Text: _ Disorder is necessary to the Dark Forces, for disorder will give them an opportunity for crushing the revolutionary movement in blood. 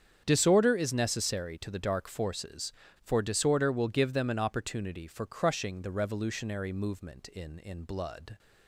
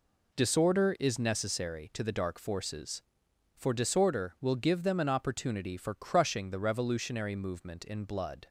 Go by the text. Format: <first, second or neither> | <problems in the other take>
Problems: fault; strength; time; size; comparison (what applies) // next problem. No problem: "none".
second | starts louder than the rest; strong; until 1.2 s; 8 dB // says "in" twice; at 7.5 s